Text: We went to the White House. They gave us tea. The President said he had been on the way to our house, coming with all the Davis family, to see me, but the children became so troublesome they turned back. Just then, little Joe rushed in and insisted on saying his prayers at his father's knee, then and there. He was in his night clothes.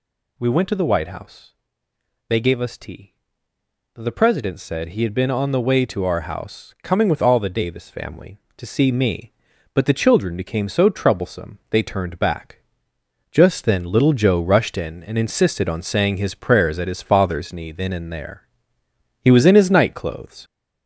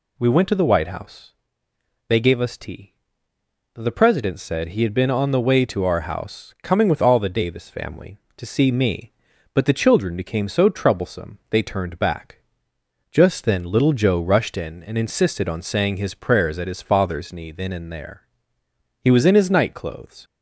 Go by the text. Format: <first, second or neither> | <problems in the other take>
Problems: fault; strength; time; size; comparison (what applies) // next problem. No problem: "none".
second | gets louder; throughout; 4 dB